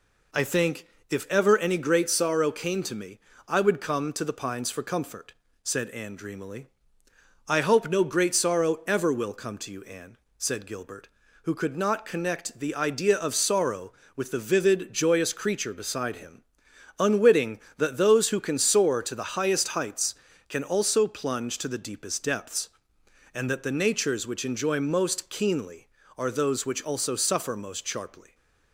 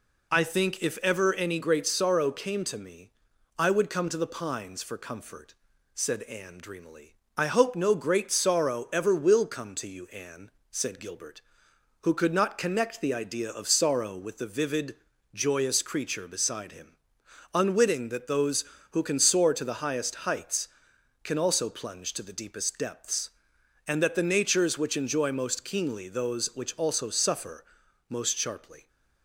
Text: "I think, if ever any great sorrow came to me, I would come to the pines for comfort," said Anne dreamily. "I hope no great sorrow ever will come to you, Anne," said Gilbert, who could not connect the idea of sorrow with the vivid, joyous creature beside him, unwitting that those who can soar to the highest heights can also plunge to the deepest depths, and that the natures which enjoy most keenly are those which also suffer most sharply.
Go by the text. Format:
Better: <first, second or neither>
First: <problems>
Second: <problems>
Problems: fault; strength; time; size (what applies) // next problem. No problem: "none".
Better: first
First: none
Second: skips "are"; at 26.0 s // pauses between "suffer" and "most"; noticeable; at 27.6 s; 0.46 s long